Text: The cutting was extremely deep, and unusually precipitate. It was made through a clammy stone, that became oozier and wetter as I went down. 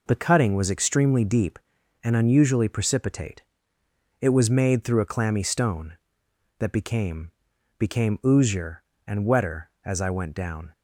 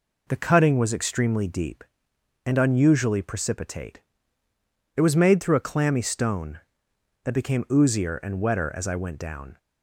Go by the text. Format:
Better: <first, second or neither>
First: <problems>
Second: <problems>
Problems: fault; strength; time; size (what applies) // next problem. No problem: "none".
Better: second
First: says "became" twice; at 7.7 s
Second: none